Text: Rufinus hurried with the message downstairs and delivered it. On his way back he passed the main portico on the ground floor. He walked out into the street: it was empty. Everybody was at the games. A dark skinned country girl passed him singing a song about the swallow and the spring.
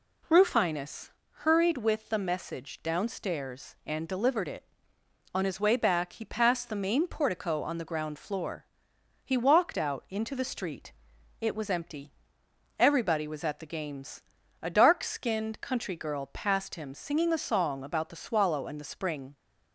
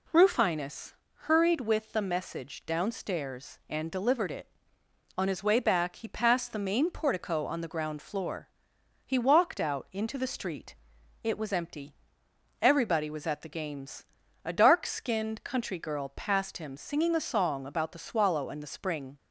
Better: neither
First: pauses between "Rufinus" and "hurried"; slight; at 1.0 s; 0.28 s long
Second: pauses between "Rufinus" and "hurried"; slight; at 0.9 s; 0.28 s long

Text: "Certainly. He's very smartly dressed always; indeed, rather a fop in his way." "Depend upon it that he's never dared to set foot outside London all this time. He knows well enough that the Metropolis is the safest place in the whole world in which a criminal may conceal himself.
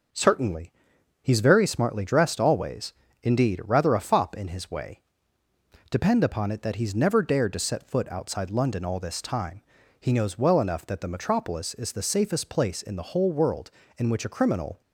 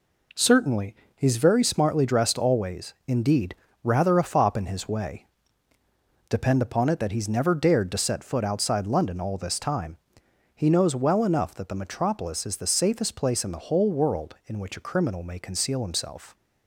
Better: second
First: starts louder than the rest; noticeable; until 1.6 s; 6 dB // stops before "may conceal himself"; at 14.8 s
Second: none

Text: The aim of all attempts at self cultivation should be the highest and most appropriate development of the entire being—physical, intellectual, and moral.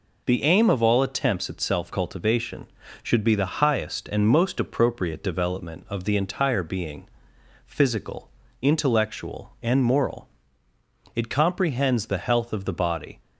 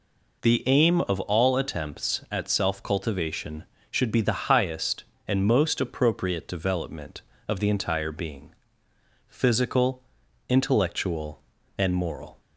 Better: second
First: goes on to say "It comprehends the health of the body"; strong; from 11.1 s on; 2.0 s long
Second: none

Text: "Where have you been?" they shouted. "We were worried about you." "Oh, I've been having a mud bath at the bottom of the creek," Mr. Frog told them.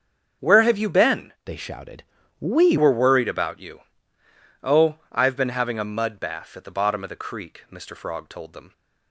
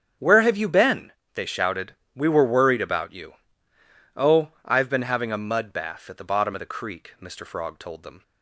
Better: second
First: starts louder than the rest; until 1.5 s; 7 dB // changes voice from "they" to "We"; from 1.4 to 2.7 s; 1.3 s long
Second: starts louder than the rest; strong; until 1.3 s; 8 dB

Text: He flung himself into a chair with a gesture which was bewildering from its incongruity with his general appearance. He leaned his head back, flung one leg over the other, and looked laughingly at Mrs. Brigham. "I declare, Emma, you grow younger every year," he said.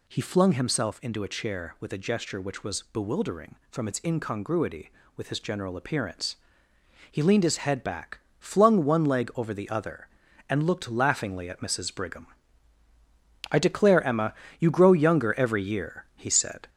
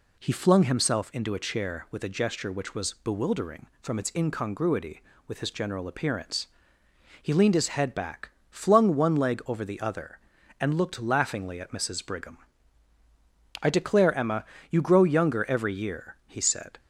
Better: second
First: gets louder; noticeable; throughout; 4 dB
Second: none

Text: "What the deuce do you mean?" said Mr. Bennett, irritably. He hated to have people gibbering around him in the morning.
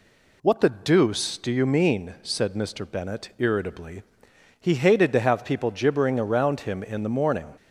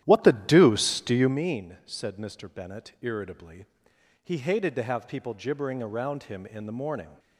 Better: first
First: none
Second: starts louder than the rest; strong; until 1.4 s; 12 dB

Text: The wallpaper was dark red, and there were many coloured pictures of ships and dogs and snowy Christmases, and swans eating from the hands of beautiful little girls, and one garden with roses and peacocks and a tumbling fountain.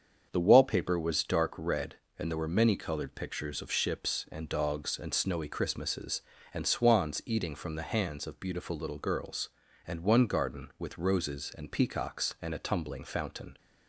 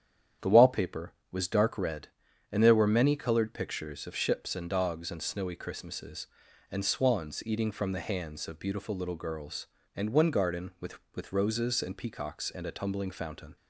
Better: first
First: starts louder than the rest; strong; until 1.3 s; 7 dB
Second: starts louder than the rest; strong; until 1.6 s; 9 dB // says "with" twice; at 11.1 s

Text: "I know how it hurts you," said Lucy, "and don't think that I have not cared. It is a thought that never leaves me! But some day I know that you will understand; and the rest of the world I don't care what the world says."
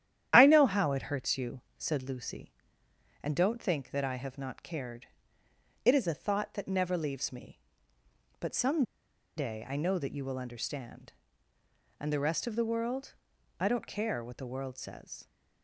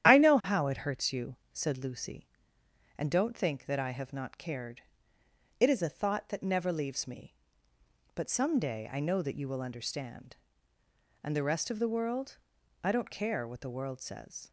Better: second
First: starts louder than the rest; strong; until 1.3 s; 10.5 dB // pauses between "some" and "day"; noticeable; at 8.8 s; 0.54 s long // pauses between "world" and "I"; at 13.1 s; 0.42 s long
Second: starts louder than the rest; strong; until 1.1 s; 11 dB // pauses between "world" and "I"; at 12.3 s; 0.42 s long

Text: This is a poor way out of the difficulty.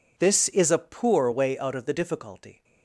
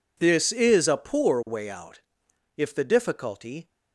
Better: first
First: none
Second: says "if" for "of"; at 2.5 s

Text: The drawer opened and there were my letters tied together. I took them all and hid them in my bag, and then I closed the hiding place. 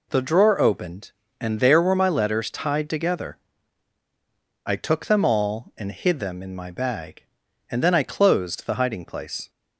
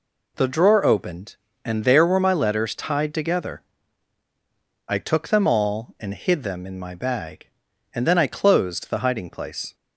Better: neither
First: none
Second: none

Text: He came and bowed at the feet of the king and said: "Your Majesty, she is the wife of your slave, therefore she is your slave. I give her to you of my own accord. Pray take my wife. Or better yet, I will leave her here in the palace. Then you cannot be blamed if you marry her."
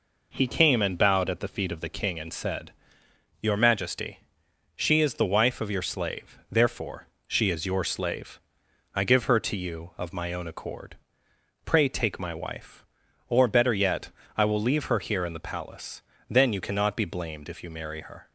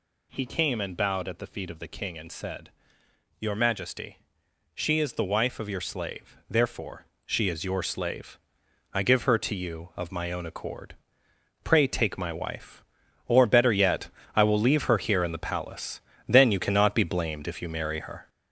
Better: first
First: pauses between "therefore" and "she"; slight; at 7.0 s; 0.22 s long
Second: gets louder; throughout; 6 dB // pauses between "therefore" and "she"; slight; at 7.0 s; 0.22 s long

